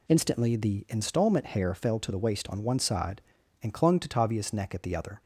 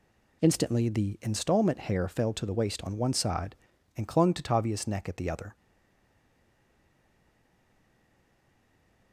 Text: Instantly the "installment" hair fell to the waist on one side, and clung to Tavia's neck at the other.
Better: first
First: none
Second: stays silent after the last word; strong; from 5.5 s on; 3.6 s long

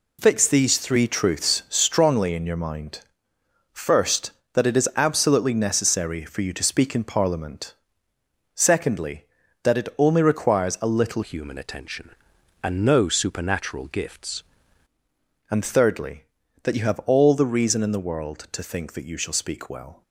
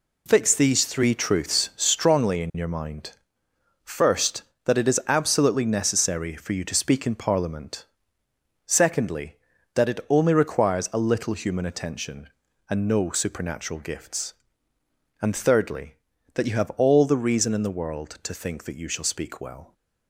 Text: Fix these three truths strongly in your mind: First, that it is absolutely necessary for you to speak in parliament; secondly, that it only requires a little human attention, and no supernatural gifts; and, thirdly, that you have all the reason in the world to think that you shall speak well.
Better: second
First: changes voice from "human" to "gifts"; from 11.2 to 14.4 s; 3.2 s long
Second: none

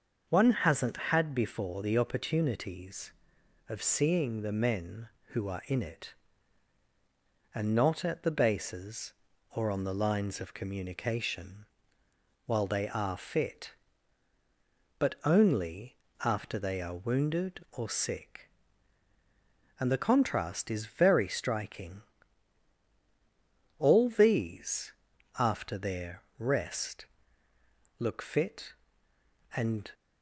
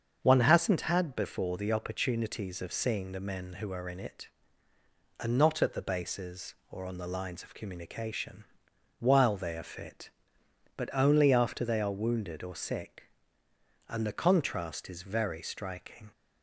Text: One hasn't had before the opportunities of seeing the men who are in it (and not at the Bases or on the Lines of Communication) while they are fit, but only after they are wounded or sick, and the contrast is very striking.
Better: second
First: starts louder than the rest; until 1.3 s; 6.5 dB // pauses between "only" and "after"; slight; at 15.9 s; 0.28 s long // goes on to say "All these after their rest look fit and"; strong; from 23.7 s on; 6.1 s long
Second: starts louder than the rest; until 1.2 s; 7 dB

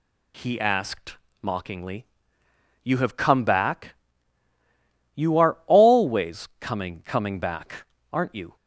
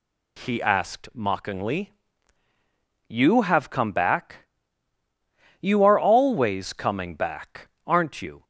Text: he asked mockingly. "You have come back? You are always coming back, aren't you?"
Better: second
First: pauses between "asked" and "mockingly"; slight; at 1.1 s; 0.26 s long // says "coming" twice; at 7.0 s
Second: none

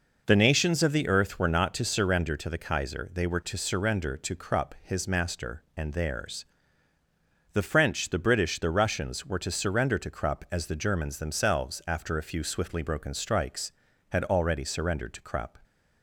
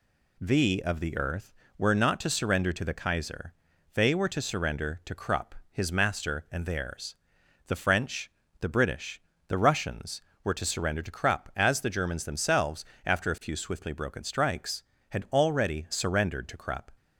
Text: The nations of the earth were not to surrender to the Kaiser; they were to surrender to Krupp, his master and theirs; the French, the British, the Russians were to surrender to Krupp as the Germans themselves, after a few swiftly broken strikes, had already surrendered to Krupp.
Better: first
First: none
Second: skips "nations"; at 0.8 s

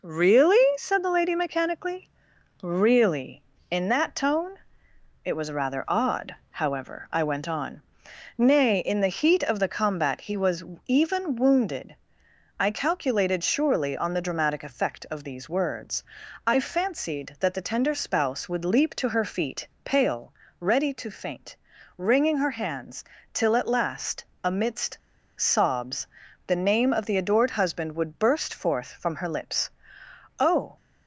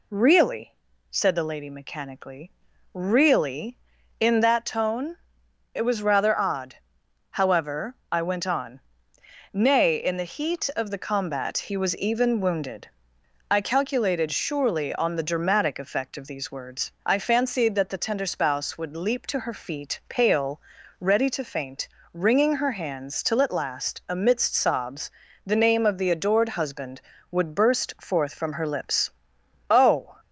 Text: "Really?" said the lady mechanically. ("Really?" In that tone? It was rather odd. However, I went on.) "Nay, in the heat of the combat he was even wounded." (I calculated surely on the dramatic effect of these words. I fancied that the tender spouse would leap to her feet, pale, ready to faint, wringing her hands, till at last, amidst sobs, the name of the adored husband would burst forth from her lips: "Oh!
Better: second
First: pauses between "was" and "even"; slight; at 10.6 s; 0.22 s long // pauses between "amidst" and "sobs"; at 24.9 s; 0.39 s long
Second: none

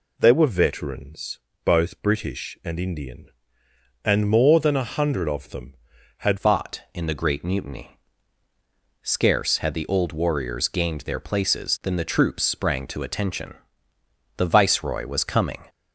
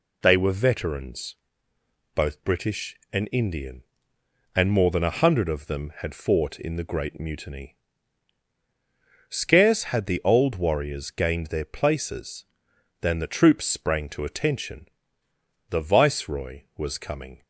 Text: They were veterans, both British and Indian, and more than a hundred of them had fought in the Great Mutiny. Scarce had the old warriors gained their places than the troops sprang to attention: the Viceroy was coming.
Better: second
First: changes voice at "fought"; from 6.3 s on; 9.3 s long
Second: none

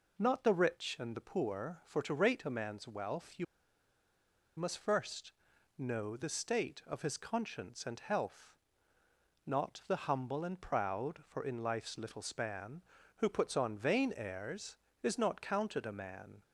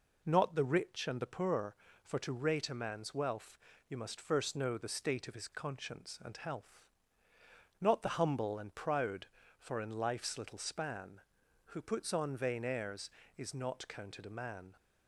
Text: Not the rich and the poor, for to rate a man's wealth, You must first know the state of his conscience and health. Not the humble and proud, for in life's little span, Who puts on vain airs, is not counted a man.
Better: second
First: pauses between "You" and "must"; at 3.4 s; 1.1 s long // pauses between "first" and "know"; noticeable; at 5.3 s; 0.46 s long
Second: none

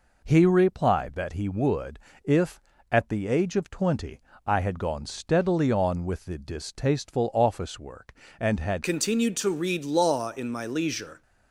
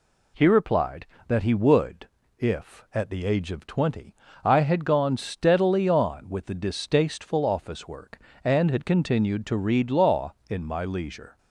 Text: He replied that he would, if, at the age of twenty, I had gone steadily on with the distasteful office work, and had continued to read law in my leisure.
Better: second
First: changes voice at "continued"; from 8.8 s on; 2.4 s long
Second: none

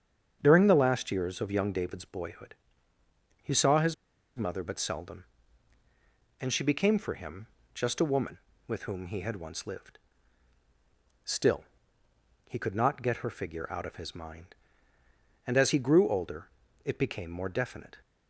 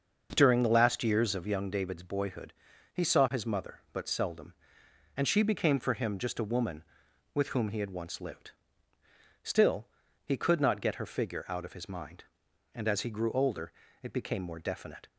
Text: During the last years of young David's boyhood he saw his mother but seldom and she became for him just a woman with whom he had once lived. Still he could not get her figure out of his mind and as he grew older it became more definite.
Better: second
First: starts louder than the rest; strong; until 1.4 s; 7.5 dB // pauses between "boyhood" and "he"; noticeable; at 2.5 s; 0.88 s long // pauses between "his" and "mother"; at 3.9 s; 0.43 s long // pauses between "him" and "just"; slight; at 7.4 s; 0.26 s long // pauses between "Still" and "he"; noticeable; at 11.6 s; 0.84 s long // pauses between "older" and "it"; slight; at 16.4 s; 0.34 s long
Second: starts louder than the rest; until 1.3 s; 6 dB // pauses between "boyhood" and "he"; at 2.5 s; 0.40 s long // pauses between "Still" and "he"; at 9.8 s; 0.38 s long // pauses between "older" and "it"; slight; at 13.7 s; 0.30 s long

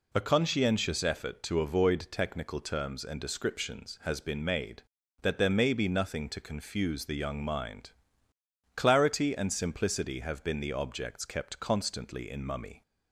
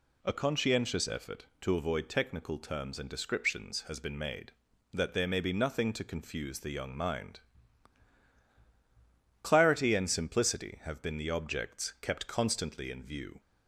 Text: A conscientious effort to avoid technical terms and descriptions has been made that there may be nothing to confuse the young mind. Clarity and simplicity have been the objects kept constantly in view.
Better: second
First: says "mummy" for "view"; at 12.4 s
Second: none

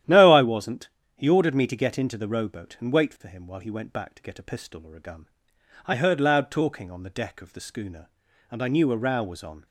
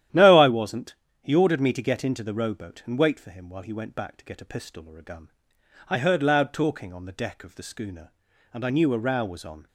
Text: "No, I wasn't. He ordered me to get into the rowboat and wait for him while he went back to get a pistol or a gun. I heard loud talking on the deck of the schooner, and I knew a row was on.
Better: neither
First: starts louder than the rest; strong; until 1.3 s; 11.5 dB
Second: starts louder than the rest; strong; until 1.3 s; 11.5 dB

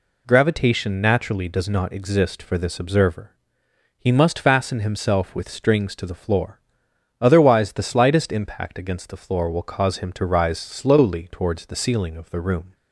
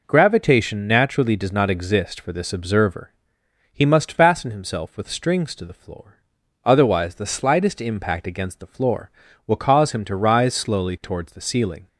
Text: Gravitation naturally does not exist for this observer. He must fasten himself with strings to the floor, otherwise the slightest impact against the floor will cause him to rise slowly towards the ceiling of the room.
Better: first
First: none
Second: stops before "of the room"; at 11.8 s

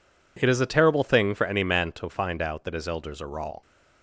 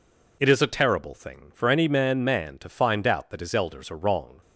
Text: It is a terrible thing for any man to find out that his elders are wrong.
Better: first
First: none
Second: says "man" twice; at 2.2 s

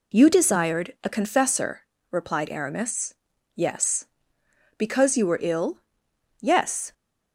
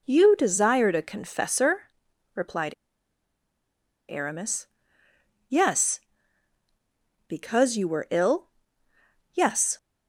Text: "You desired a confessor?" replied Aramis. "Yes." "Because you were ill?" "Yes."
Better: first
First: none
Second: pauses between "replied" and "Aramis"; strong; at 2.7 s; 1.3 s long

